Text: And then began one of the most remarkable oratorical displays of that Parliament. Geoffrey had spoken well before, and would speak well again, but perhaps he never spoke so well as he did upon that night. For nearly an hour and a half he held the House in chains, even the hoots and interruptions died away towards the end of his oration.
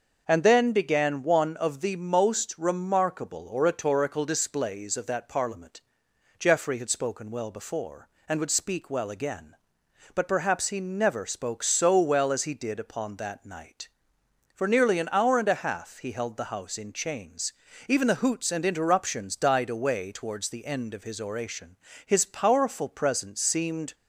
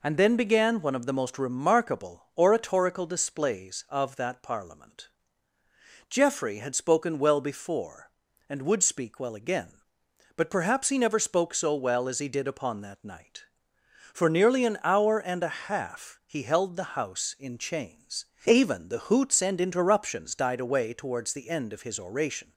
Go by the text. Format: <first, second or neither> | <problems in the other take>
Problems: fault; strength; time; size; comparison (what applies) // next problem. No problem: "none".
second | starts louder than the rest; noticeable; until 1.2 s; 6 dB // goes on to say "His powerful presence seemed"; strong; from 22.0 s on; 1.8 s long